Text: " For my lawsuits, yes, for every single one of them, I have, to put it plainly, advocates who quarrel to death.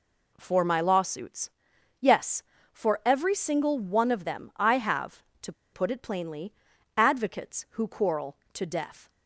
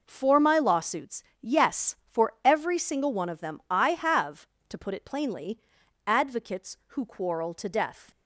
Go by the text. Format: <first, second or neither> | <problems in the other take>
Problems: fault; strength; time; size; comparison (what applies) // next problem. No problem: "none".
second | pauses between "to" and "put"; slight; at 5.5 s; 0.20 s long